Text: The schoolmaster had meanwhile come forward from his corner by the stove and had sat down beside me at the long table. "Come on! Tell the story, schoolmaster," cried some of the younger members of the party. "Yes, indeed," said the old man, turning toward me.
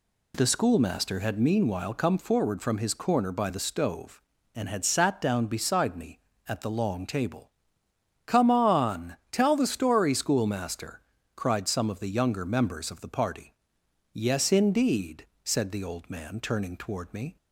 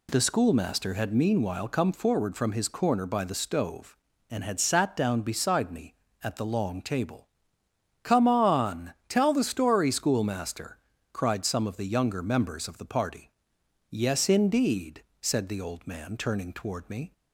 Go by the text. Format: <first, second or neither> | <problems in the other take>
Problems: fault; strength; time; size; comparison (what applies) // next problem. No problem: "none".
neither | none